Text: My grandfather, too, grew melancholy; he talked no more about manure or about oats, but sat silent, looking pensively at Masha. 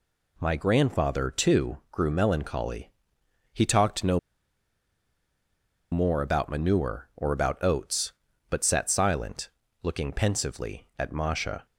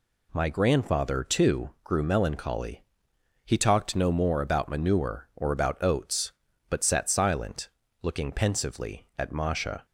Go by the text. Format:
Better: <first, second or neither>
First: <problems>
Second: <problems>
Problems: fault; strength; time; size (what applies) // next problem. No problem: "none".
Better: second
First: pauses between "no" and "more"; strong; at 4.1 s; 1.7 s long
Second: none